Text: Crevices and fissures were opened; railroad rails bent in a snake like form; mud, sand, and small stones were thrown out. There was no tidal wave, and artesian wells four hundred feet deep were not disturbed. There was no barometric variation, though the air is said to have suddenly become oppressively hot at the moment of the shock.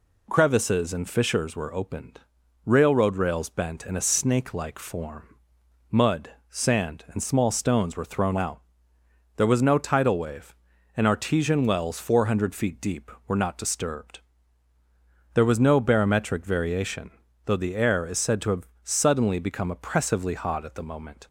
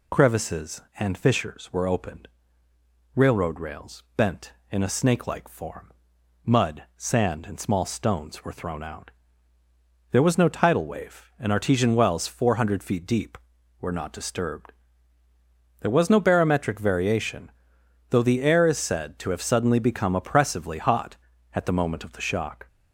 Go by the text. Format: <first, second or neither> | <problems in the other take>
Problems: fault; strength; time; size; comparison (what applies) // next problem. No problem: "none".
second | pauses between "have" and "suddenly"; slight; at 18.6 s; 0.16 s long // stops before "of the shock"; at 21.2 s